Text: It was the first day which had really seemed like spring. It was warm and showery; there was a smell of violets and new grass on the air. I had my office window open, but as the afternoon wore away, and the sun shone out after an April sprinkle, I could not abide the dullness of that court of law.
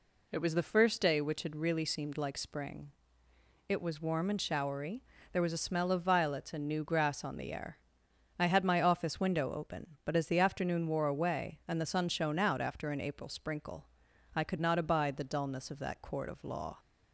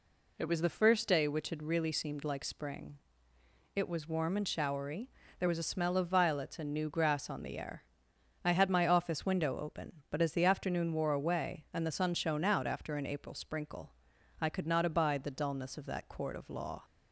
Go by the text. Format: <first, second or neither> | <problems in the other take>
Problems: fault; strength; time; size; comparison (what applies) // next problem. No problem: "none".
neither | none